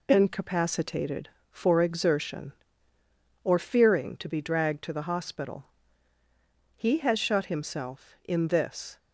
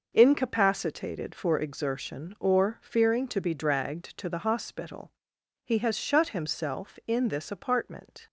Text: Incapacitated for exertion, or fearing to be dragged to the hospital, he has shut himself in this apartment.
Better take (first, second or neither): second